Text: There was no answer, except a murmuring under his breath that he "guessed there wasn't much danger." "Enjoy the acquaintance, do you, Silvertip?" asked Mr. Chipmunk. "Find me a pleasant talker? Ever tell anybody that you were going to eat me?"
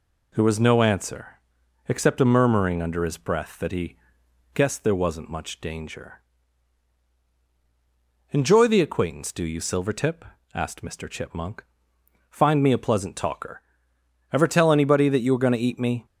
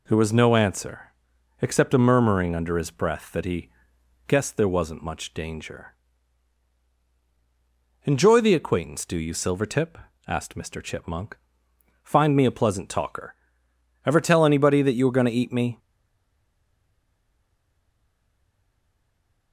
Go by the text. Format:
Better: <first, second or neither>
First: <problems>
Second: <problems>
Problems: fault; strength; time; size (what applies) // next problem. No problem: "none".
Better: first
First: pauses between "he" and "guessed"; noticeable; at 3.9 s; 0.56 s long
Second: pauses between "he" and "guessed"; noticeable; at 3.7 s; 0.56 s long // stays silent after the last word; strong; from 15.7 s on; 3.8 s long